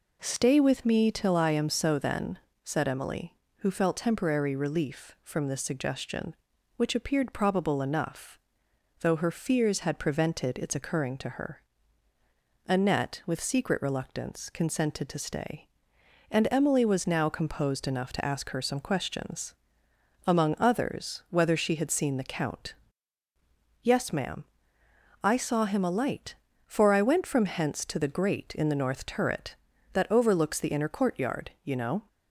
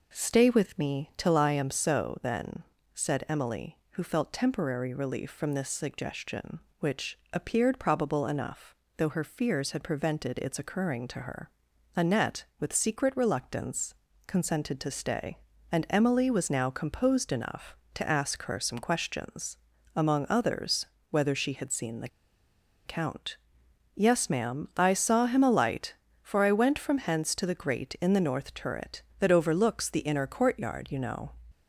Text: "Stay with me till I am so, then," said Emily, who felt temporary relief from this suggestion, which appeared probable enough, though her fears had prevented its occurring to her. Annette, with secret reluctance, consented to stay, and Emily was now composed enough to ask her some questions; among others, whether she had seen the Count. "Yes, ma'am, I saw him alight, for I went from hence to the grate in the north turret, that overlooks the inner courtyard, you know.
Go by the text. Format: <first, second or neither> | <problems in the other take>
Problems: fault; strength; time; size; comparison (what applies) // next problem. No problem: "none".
first | pauses between "which" and "appeared"; slight; at 7.1 s; 0.16 s long // pauses between "the" and "Count"; noticeable; at 22.0 s; 0.77 s long